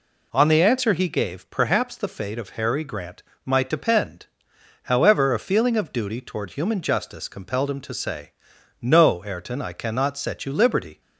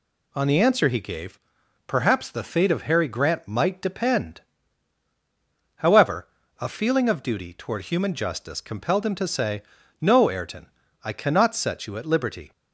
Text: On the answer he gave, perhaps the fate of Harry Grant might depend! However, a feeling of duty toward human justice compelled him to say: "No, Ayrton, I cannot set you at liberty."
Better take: second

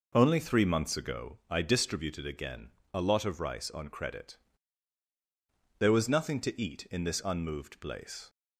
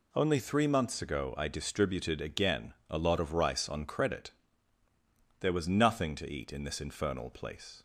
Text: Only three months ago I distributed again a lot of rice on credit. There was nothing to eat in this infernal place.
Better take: second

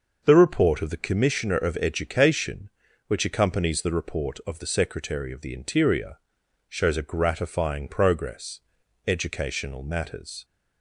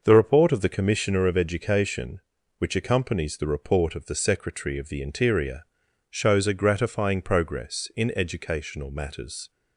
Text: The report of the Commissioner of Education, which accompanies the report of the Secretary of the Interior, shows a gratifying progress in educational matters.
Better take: second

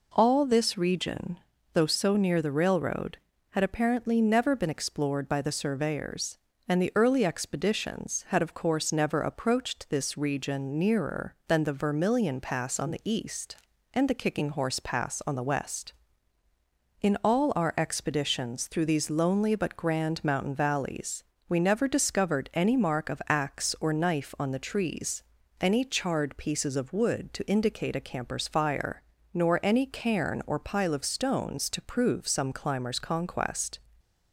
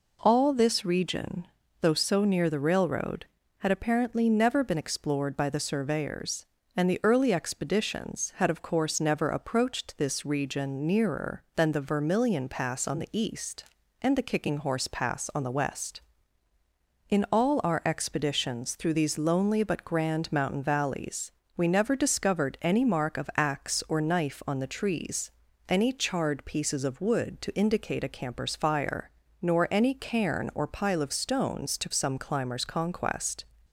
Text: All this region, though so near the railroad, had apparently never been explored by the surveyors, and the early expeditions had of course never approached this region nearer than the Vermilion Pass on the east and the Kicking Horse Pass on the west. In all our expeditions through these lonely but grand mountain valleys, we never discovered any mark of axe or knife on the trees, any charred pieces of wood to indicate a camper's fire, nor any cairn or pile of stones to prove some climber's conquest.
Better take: first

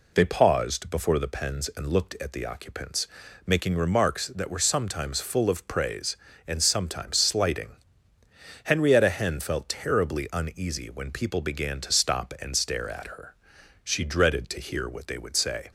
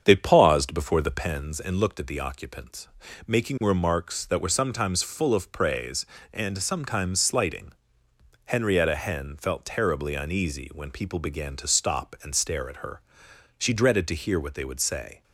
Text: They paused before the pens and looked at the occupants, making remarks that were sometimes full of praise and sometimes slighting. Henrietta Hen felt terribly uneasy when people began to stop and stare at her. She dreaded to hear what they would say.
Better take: first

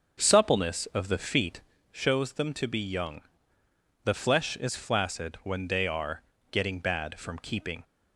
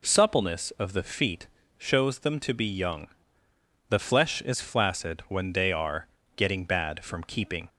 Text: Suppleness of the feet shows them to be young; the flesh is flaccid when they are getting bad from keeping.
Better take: second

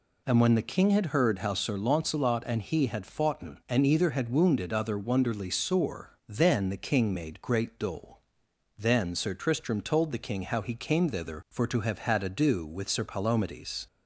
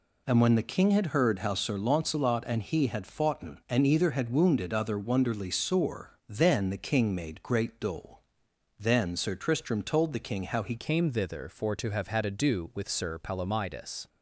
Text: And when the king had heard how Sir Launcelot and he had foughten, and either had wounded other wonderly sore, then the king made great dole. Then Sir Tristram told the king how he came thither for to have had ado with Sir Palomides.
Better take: first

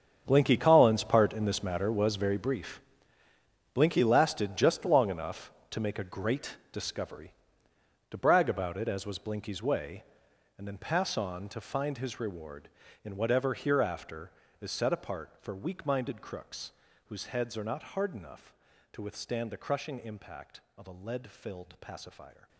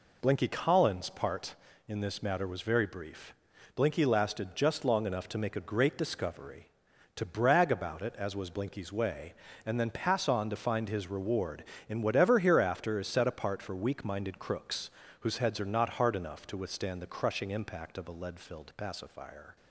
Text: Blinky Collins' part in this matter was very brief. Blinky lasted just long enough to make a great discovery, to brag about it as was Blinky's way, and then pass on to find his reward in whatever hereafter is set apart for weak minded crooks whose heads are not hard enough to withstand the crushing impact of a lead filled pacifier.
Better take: second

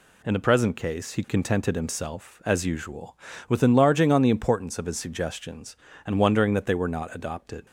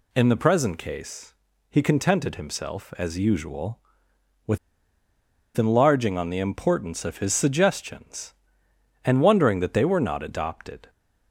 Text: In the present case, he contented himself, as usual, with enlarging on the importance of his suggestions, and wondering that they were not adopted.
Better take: first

